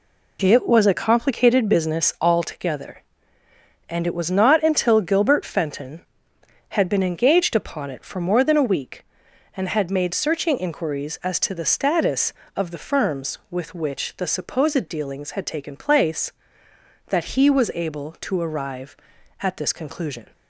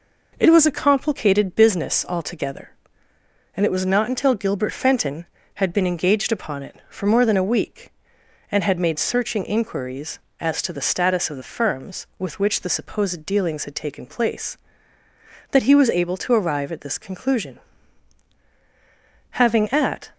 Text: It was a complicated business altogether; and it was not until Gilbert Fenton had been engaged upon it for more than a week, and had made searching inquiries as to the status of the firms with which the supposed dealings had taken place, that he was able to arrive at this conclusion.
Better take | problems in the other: first | goes on to say "Having at"; noticeable; from 19.3 s on; 0.80 s long

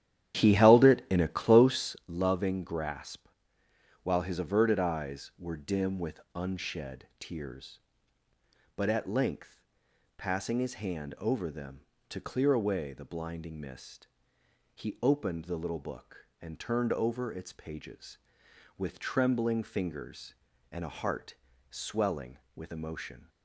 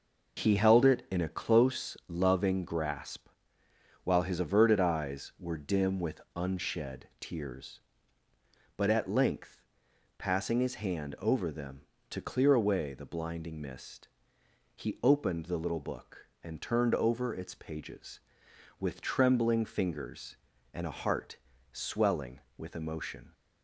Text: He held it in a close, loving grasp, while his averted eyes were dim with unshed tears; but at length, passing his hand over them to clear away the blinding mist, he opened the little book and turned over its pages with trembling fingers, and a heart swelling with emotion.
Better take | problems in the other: second | starts louder than the rest; strong; until 2.1 s; 11 dB // pauses between "heart" and "swelling"; slight; at 21.3 s; 0.34 s long; slight in the second

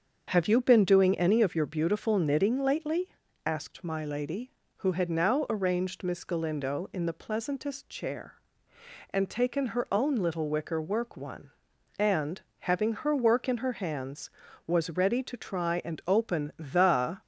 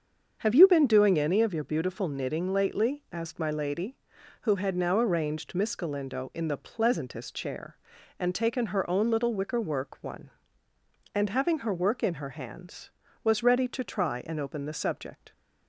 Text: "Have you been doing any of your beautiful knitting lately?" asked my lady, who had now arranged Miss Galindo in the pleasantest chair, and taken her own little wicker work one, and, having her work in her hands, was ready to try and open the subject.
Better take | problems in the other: second | starts louder than the rest; until 1.3 s; 7 dB; also in the second // stops before "subject"; at 17.2 s

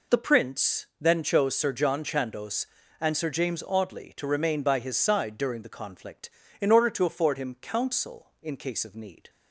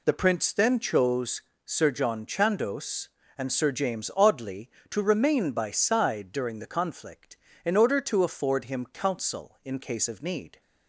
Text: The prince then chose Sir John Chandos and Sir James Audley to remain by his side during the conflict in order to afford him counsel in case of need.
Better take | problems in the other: first | pauses between "chose" and "Sir"; slight; at 1.4 s; 0.24 s long // skips "his"; at 5.6 s

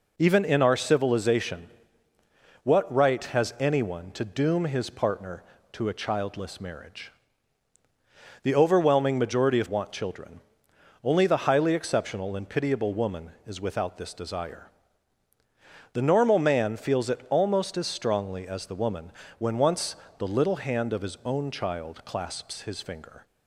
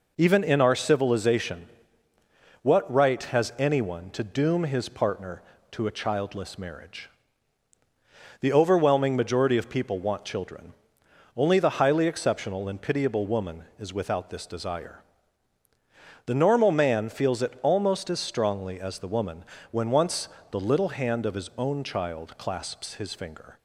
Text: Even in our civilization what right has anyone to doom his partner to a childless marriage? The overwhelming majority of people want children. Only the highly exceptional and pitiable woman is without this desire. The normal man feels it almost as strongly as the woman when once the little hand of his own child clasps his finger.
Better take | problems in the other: second | pauses between "civilization" and "what"; noticeable; at 1.6 s; 0.96 s long; noticeable in the second // skips "people"; at 9.6 s // pauses between "woman" and "when"; slight; at 19.1 s; 0.26 s long; slight in the second // pauses between "once" and "the"; slight; at 19.9 s; 0.22 s long; slight in the second

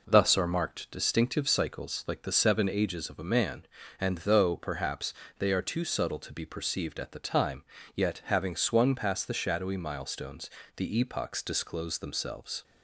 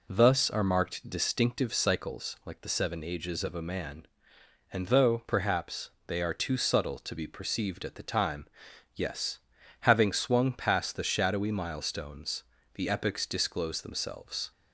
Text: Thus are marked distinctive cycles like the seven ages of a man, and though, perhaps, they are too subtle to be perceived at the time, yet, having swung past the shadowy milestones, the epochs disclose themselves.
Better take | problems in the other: first | says "yes" for "yet"; at 8.9 s

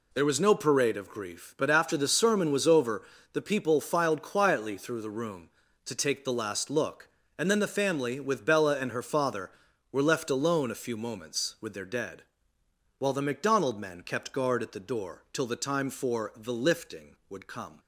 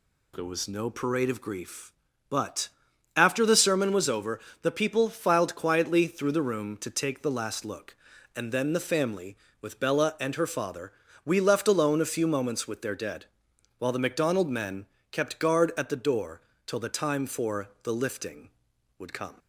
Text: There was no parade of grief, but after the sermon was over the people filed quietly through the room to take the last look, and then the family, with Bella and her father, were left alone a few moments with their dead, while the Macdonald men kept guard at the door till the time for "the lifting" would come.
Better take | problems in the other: first | pauses between "but" and "after"; noticeable; at 2.6 s; 0.46 s long // pauses between "over" and "the"; slight; at 4.4 s; 0.22 s long; slight in the first // says "we" for "were"; at 11.2 s // pauses between "men" and "kept"; slight; at 14.8 s; 0.26 s long // pauses between "door" and "till"; slight; at 16.4 s; 0.26 s long // pauses between "for" and "the"; slight; at 17.6 s; 0.16 s long

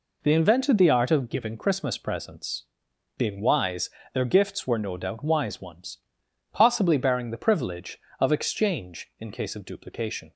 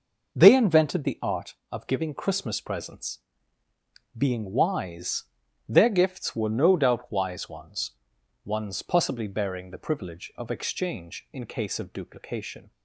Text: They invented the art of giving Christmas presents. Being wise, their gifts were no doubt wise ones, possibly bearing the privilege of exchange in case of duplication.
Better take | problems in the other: first | says "ones" twice; at 8.4 s

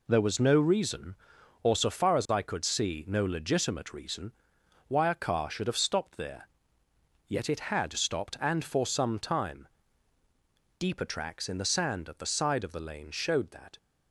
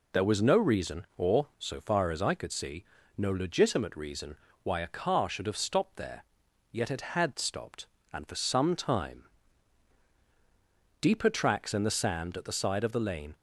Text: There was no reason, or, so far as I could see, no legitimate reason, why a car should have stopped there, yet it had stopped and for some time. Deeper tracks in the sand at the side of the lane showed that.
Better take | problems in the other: first | stops before "showed that"; at 13.3 s

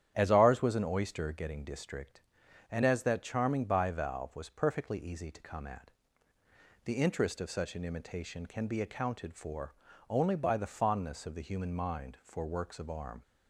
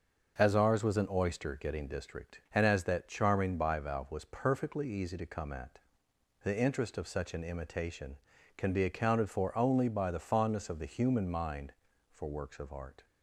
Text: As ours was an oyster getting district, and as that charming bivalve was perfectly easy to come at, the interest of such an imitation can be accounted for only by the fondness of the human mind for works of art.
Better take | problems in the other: second | starts louder than the rest; strong; until 1.1 s; 10 dB; also in the second // pauses between "for" and "only"; slight; at 9.7 s; 0.36 s long // says "arm" for "art"; at 12.8 s

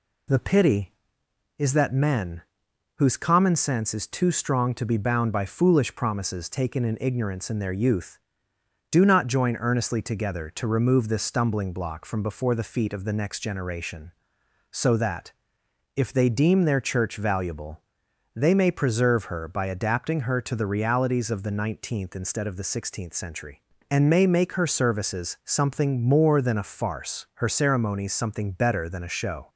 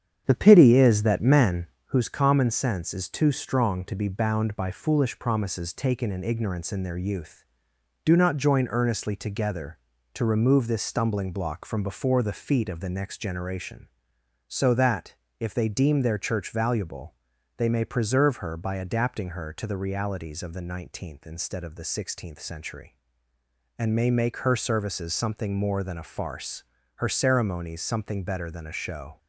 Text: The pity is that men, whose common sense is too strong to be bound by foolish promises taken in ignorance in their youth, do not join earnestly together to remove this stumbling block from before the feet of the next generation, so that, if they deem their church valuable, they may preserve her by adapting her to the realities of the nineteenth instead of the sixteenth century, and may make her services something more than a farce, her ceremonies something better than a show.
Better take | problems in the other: first | starts louder than the rest; strong; until 2.0 s; 8.5 dB

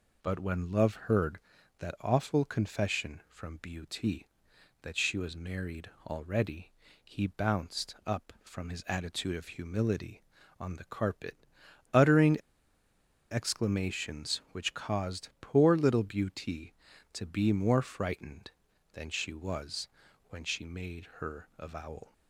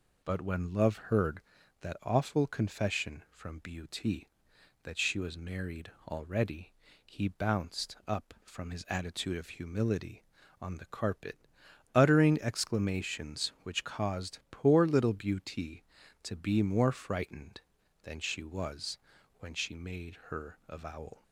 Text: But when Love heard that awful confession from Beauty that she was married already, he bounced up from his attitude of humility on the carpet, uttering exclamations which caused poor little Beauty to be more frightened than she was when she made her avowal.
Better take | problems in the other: second | pauses between "married" and "already"; slight; at 5.9 s; 0.16 s long; slight in the second // pauses between "uttering" and "exclamations"; noticeable; at 12.3 s; 0.92 s long // pauses between "was" and "when"; at 19.8 s; 0.40 s long; also in the second

